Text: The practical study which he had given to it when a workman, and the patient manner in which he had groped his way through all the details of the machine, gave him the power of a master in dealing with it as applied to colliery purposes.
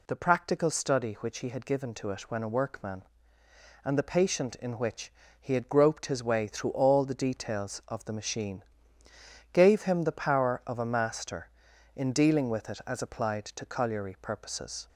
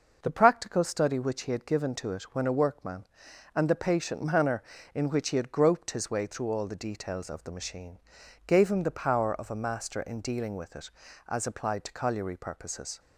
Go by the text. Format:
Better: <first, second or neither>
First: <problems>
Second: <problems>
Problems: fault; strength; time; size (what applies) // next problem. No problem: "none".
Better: second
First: skips "manner"; at 4.5 s // pauses between "which" and "he"; slight; at 5.1 s; 0.28 s long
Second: none